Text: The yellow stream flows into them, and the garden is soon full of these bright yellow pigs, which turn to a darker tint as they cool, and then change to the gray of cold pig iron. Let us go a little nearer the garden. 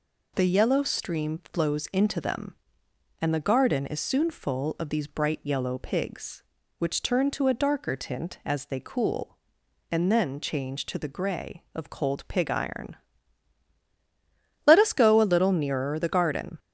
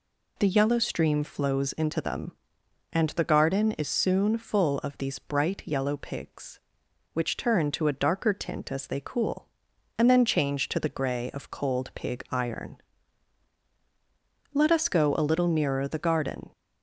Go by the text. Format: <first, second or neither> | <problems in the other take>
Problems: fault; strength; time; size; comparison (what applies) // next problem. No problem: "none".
neither | none